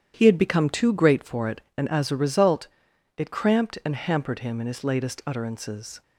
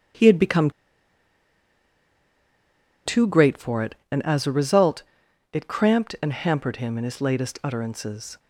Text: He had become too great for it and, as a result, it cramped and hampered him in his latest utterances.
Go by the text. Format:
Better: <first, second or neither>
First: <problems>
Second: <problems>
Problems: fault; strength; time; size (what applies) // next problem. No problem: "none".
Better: first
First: starts louder than the rest; strong; until 1.1 s; 10 dB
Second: starts louder than the rest; strong; until 3.5 s; 10 dB // pauses between "become" and "too"; strong; at 0.6 s; 2.3 s long